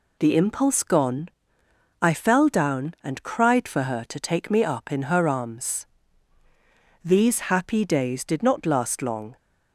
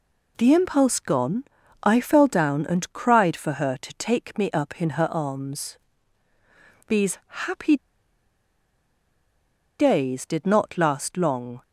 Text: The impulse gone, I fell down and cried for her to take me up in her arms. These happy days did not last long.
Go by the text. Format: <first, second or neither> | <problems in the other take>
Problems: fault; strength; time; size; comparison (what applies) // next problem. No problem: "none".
first | pauses between "These" and "happy"; slight; at 7.1 s; 0.26 s long // pauses between "happy" and "days"; strong; at 7.7 s; 2.0 s long